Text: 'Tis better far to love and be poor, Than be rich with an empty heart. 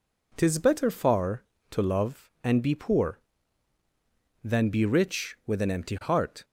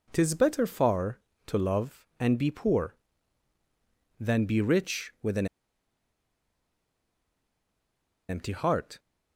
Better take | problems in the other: first | pauses between "an" and "empty"; strong; at 5.4 s; 2.8 s long

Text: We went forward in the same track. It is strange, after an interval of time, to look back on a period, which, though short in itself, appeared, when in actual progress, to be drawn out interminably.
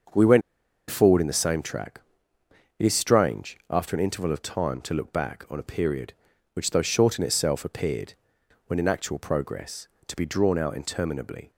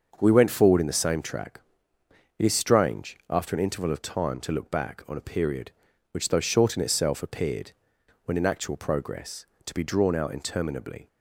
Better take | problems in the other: second | starts louder than the rest; until 1.6 s; 6.5 dB; also in the second // pauses between "went" and "forward"; noticeable; at 0.4 s; 0.48 s long

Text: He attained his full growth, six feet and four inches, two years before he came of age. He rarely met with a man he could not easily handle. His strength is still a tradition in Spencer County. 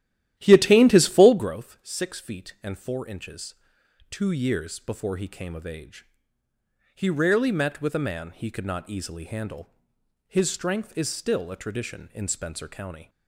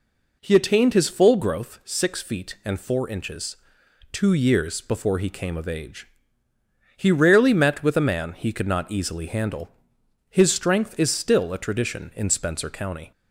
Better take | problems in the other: second | starts louder than the rest; strong; until 1.5 s; 13 dB

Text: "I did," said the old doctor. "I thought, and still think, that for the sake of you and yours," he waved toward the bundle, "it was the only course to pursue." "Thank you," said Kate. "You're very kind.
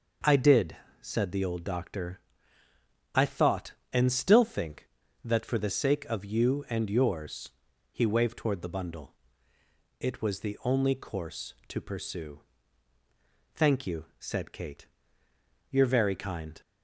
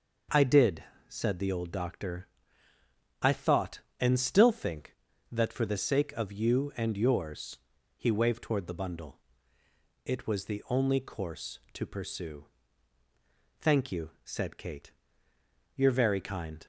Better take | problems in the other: neither | none

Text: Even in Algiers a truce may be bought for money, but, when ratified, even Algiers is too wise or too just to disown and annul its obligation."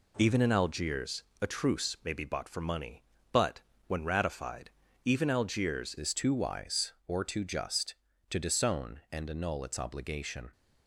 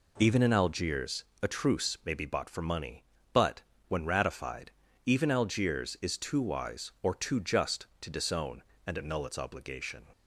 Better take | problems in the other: second | pauses between "Algiers" and "a"; slight; at 1.2 s; 0.18 s long; slight in the second // changes voice at "is"; from 5.9 s on; 4.6 s long

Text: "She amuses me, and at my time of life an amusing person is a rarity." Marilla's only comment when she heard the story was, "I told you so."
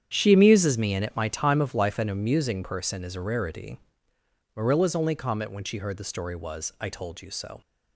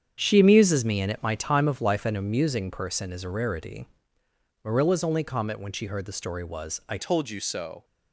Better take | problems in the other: first | starts louder than the rest; strong; until 1.2 s; 8 dB; strong in the first // changes voice at "told"; from 6.9 s on; 0.9 s long

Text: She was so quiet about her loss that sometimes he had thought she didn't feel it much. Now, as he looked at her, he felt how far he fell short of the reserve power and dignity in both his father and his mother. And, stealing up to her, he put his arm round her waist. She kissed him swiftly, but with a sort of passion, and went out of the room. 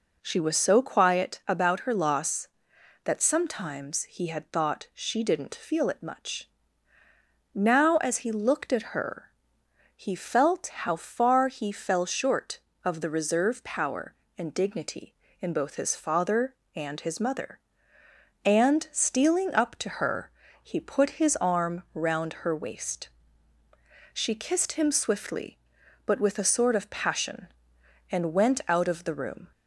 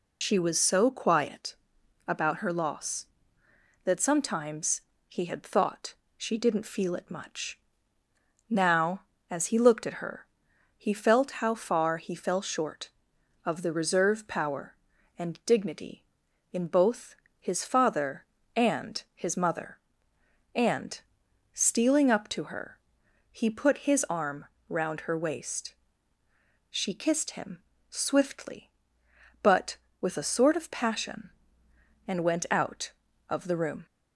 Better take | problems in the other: first | loses the start of "She"; at 0.2 s; 75 ms // pauses between "quiet" and "about"; noticeable; at 1.5 s; 0.52 s long // pauses between "sometimes" and "he"; slight; at 4.8 s; 0.26 s long // pauses between "thought" and "she"; slight; at 5.9 s; 0.22 s long // pauses between "both" and "his"; slight; at 17.1 s; 0.24 s long // pauses between "arm" and "round"; slight; at 24.4 s; 0.24 s long // pauses between "him" and "swiftly"; slight; at 27.5 s; 0.30 s long

